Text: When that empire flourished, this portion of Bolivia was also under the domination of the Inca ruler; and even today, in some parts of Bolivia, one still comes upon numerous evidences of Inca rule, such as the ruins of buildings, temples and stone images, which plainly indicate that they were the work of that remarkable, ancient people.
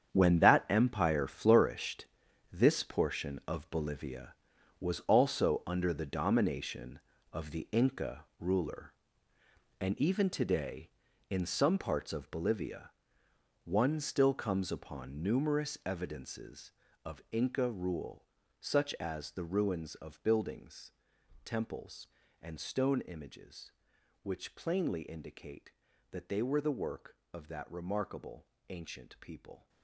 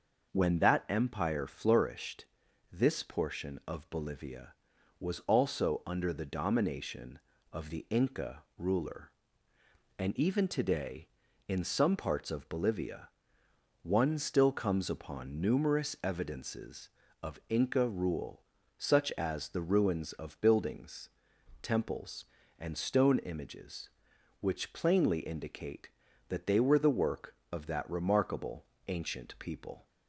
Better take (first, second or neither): second